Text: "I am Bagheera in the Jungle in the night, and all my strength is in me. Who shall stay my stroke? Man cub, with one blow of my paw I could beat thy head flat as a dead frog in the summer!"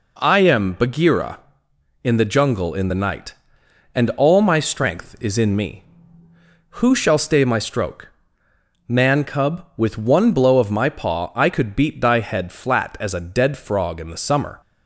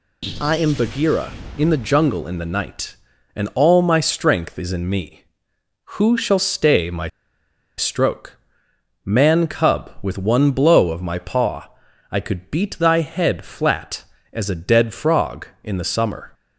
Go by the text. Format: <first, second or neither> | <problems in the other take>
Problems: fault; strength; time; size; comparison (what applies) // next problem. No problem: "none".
first | pauses between "my" and "stroke"; noticeable; at 7.0 s; 0.68 s long // pauses between "paw" and "I"; at 11.6 s; 0.42 s long